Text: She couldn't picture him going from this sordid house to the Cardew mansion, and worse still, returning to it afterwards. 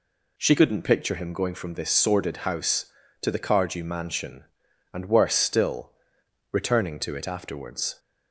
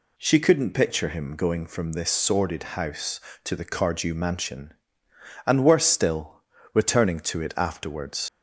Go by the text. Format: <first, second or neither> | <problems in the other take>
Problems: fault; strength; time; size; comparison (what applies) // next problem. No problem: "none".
first | leaves "afterwards" unfinished; at 8.2 s; 95 ms